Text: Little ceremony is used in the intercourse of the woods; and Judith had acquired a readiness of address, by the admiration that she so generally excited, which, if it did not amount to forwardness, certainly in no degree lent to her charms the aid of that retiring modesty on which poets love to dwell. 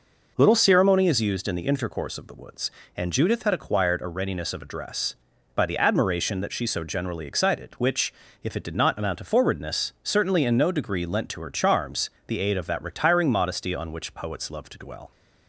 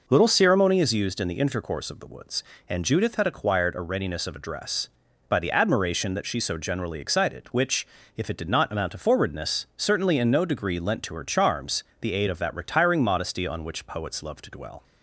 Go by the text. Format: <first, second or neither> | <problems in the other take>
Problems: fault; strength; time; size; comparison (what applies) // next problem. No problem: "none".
neither | pauses between "charms" and "the"; slight; the same in both